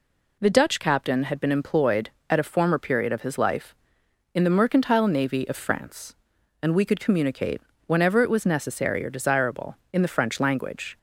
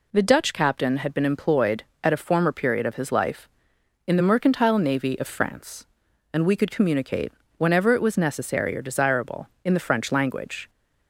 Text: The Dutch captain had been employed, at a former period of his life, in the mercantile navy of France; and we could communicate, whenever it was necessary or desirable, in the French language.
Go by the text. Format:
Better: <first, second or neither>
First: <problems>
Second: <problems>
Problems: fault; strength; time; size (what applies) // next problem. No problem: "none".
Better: neither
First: none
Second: none